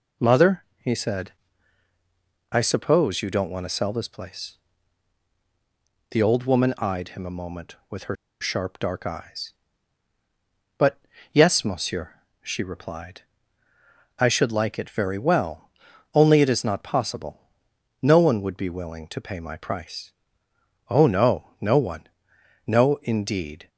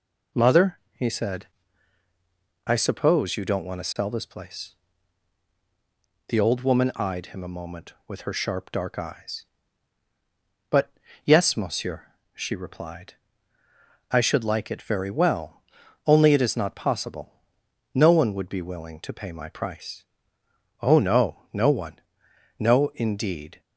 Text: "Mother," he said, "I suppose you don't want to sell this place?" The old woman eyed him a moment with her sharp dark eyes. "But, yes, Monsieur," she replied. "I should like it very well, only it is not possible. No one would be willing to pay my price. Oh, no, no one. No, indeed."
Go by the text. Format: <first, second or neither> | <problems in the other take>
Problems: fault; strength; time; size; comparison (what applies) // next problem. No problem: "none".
second | pauses between "her" and "sharp"; slight; at 8.1 s; 0.25 s long